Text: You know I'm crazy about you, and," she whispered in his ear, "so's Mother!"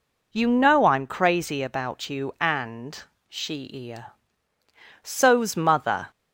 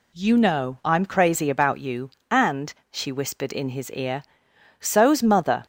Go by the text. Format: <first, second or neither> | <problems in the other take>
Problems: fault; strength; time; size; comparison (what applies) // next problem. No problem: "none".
second | skips "whispered in his"; at 3.6 s